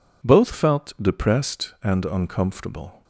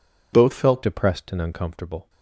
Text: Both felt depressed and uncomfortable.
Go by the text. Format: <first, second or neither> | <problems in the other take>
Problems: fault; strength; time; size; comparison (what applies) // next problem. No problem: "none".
first | changes voice at "depressed"; from 0.8 s on; 1.2 s long